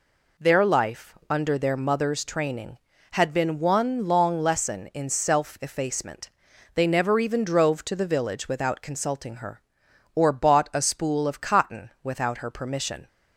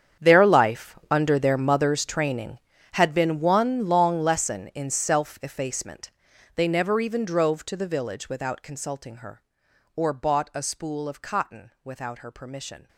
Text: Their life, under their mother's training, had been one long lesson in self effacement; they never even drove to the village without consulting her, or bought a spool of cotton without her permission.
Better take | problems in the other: first | gets quieter; strong; throughout; 17 dB

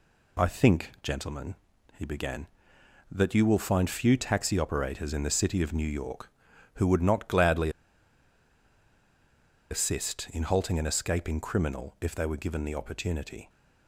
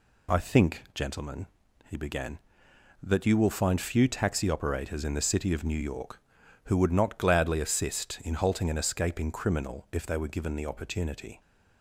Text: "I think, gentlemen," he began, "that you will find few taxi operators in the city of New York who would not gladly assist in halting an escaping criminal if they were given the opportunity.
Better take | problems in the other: second | pauses between "gladly" and "assist"; strong; at 7.6 s; 2.0 s long

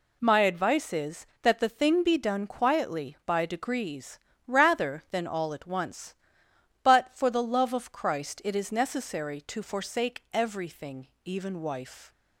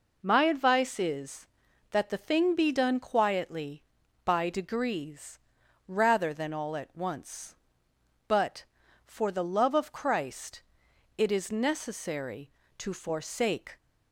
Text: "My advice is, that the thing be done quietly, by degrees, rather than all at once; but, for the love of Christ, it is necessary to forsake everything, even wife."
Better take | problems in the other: first | stops before "everything even wife"; at 13.7 s

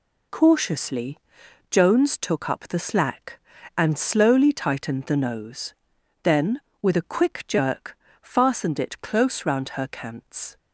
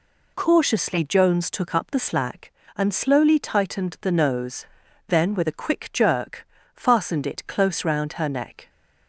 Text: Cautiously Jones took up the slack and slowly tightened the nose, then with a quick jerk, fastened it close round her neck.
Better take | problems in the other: second | pauses between "Cautiously" and "Jones"; noticeable; at 1.1 s; 0.52 s long // says "cants" for "neck"; at 9.8 s

